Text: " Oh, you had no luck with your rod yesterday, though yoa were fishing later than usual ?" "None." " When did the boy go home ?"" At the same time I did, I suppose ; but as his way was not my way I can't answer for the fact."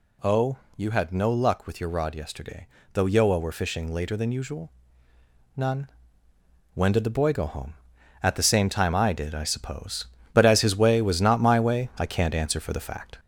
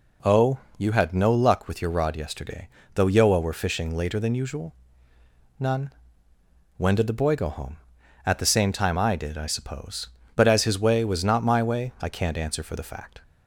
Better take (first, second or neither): second